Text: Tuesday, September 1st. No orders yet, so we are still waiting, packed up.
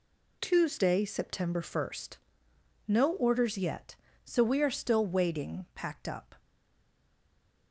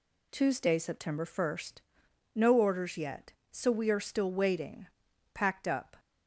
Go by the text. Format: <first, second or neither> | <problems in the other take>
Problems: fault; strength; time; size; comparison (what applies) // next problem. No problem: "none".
second | stays silent after the last word; noticeable; from 6.3 s on; 1.4 s long